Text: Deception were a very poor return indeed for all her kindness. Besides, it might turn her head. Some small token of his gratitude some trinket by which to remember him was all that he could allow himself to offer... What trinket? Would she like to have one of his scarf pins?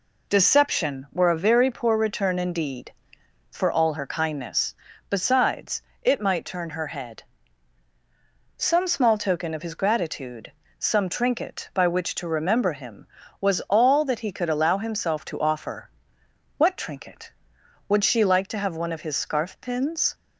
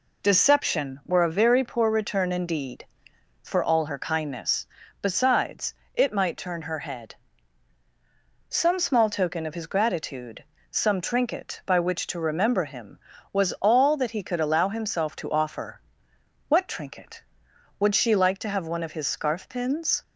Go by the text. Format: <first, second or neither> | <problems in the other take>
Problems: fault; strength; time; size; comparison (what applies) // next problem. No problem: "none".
neither | pauses between "gratitude" and "some"; slight; the same in both